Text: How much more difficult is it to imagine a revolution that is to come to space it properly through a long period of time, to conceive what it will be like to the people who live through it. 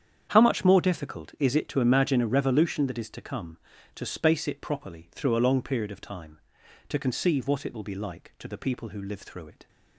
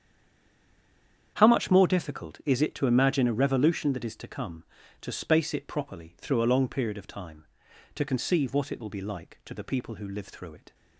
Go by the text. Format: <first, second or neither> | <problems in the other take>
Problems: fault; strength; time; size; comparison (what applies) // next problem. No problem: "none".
first | stays silent before the first word; noticeable; until 1.3 s; 1.3 s long // starts louder than the rest; strong; until 2.3 s; 8.5 dB; strong in the first